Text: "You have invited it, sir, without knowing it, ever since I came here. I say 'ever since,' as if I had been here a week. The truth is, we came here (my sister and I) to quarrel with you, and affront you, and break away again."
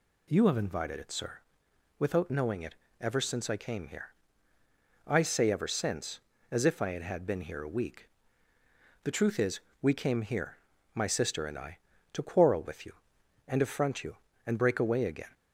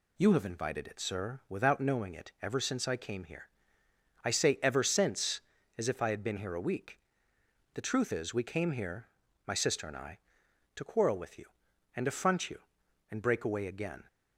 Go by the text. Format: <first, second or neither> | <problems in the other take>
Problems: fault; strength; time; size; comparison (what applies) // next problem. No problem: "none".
second | says "had" twice; at 7.0 s